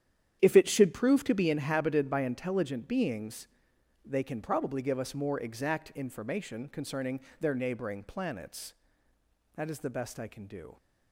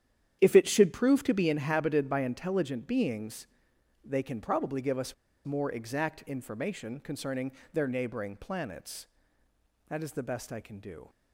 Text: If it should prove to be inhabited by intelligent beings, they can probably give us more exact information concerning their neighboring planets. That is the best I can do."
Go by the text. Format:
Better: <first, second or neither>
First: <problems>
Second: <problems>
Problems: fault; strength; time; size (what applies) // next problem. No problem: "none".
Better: first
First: starts louder than the rest; strong; until 1.4 s; 9.5 dB // pauses between "concerning" and "their"; slight; at 7.1 s; 0.20 s long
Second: starts louder than the rest; strong; until 1.4 s; 9.5 dB // pauses between "us" and "more"; slight; at 5.1 s; 0.30 s long // pauses between "concerning" and "their"; slight; at 7.5 s; 0.22 s long